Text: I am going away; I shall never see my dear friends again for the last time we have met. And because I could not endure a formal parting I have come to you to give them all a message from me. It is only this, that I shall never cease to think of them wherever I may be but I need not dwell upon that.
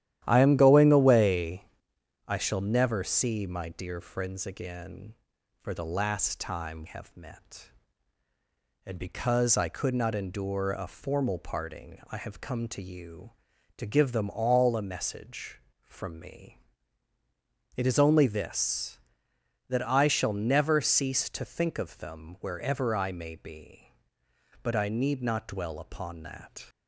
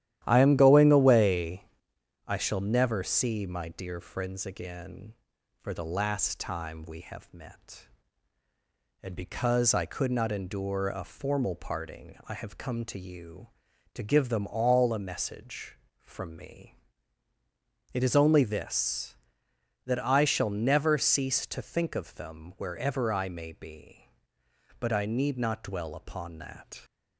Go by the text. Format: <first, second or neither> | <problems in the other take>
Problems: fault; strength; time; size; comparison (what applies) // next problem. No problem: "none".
second | starts louder than the rest; strong; until 1.2 s; 12.5 dB; strong in the second // skips "we"; at 6.8 s